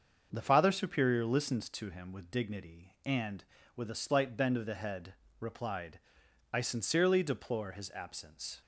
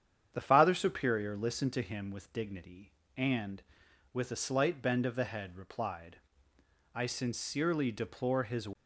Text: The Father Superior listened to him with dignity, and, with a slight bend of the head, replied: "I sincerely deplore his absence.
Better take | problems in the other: first | starts louder than the rest; strong; until 1.3 s; 8.5 dB; also in the first // stops before "absence"; at 8.7 s

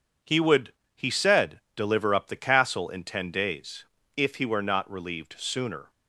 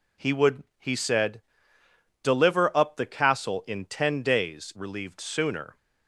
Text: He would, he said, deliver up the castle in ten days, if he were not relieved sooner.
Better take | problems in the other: first | skips "if he were not"; at 4.7 s

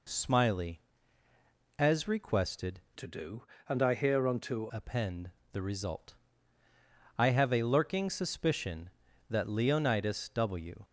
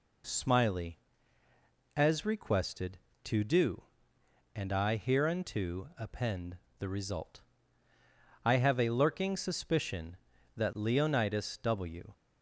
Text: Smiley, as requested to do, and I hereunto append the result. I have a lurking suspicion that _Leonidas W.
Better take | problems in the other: second | changes voice from "to" to "hereunto"; from 2.9 to 4.6 s; 1.7 s long // pauses between "append" and "the"; slight; at 5.3 s; 0.22 s long; slight in the second

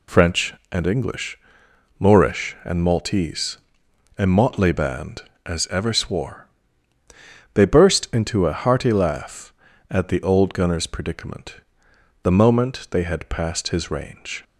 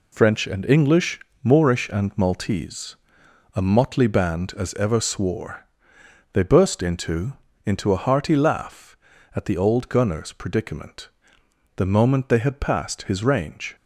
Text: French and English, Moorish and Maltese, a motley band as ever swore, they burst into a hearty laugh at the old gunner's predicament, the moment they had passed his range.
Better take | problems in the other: first | says "into" twice; at 7.6 s

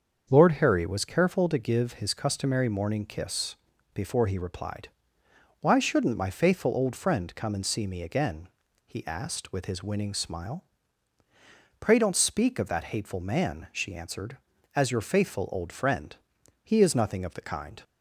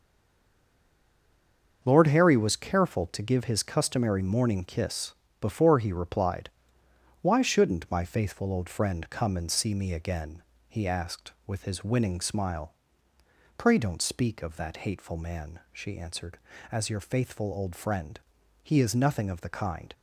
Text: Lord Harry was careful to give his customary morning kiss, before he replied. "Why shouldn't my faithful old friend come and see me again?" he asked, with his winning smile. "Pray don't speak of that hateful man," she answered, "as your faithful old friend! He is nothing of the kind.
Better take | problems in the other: first | stays silent before the first word; noticeable; until 1.8 s; 1.8 s long // starts louder than the rest; until 2.8 s; 6.5 dB; also in the first

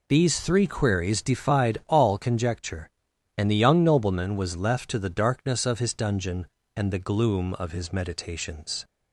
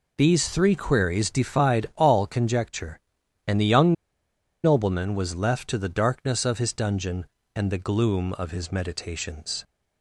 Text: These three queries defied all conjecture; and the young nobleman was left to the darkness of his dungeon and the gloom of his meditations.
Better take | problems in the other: first | pauses between "young" and "nobleman"; noticeable; at 3.9 s; 0.71 s long

